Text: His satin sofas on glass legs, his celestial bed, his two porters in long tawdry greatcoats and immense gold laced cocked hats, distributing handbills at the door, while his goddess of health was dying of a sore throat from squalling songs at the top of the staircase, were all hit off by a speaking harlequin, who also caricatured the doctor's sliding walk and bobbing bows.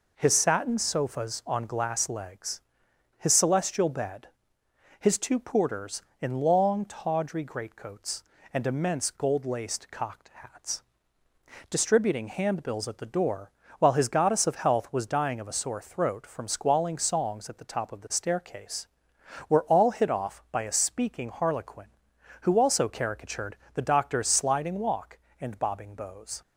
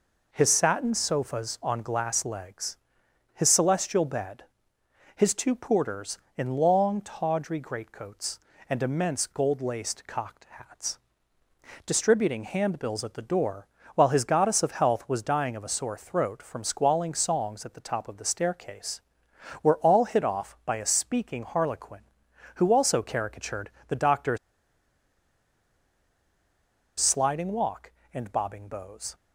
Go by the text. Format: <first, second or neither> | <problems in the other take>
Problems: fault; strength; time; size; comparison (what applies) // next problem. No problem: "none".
first | pauses between "caricatured" and "the"; slight; at 23.6 s; 0.20 s long; slight in the first // pauses between "doctor's" and "sliding"; strong; at 24.3 s; 2.6 s long